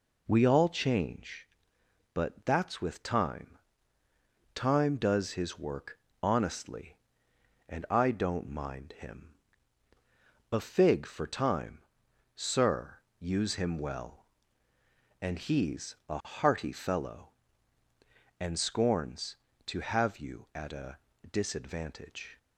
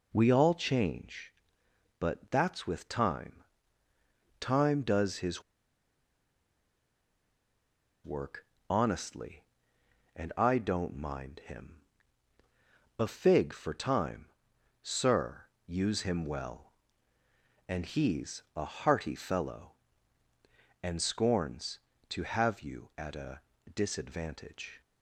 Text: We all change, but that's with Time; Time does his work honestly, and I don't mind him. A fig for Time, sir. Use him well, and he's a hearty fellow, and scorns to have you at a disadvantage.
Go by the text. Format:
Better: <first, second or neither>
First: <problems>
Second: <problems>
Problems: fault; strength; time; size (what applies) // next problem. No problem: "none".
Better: first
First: pauses between "work" and "honestly"; slight; at 5.9 s; 0.20 s long // pauses between "he's" and "a"; slight; at 15.9 s; 0.16 s long // pauses between "a" and "disadvantage"; slight; at 20.9 s; 0.34 s long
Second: pauses between "his" and "work"; strong; at 5.4 s; 2.6 s long // pauses between "work" and "honestly"; slight; at 8.4 s; 0.20 s long // pauses between "he's" and "a"; slight; at 18.4 s; 0.16 s long // pauses between "a" and "disadvantage"; slight; at 23.4 s; 0.34 s long